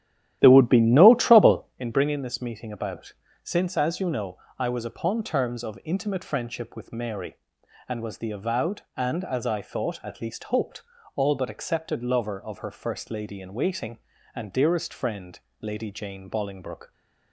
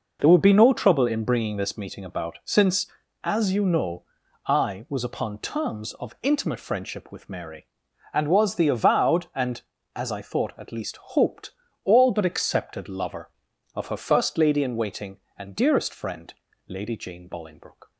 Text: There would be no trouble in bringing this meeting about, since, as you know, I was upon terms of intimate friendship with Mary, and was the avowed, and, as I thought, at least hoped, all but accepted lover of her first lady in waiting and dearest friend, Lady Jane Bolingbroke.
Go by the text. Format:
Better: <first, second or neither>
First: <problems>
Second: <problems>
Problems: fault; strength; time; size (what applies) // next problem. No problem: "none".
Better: second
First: starts louder than the rest; strong; until 1.8 s; 12 dB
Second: none